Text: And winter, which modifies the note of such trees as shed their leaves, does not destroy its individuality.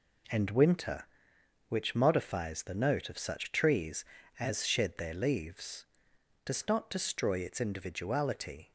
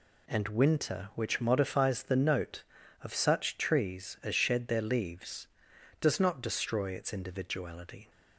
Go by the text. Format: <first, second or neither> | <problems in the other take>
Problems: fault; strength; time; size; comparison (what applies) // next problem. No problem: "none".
neither | none